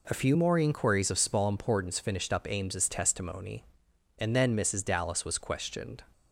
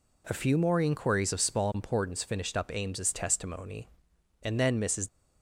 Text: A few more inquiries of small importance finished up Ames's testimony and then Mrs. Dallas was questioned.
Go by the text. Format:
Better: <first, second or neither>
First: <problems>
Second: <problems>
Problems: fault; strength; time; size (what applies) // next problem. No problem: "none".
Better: first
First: none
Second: stops before "Dallas was questioned"; at 5.0 s